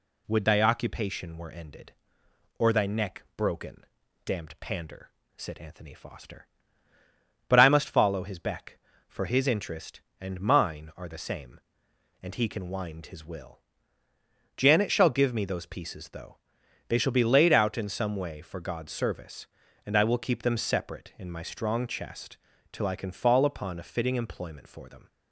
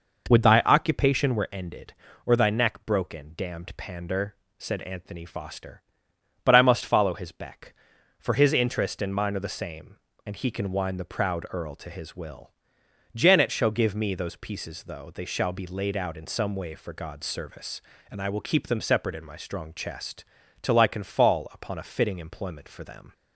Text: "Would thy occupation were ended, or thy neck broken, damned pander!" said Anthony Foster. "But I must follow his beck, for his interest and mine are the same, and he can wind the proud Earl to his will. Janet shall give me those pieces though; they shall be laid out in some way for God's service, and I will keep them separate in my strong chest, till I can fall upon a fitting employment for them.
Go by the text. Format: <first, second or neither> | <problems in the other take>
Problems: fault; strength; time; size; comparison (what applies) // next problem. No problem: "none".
second | skips "the proud Earl to"; at 13.0 s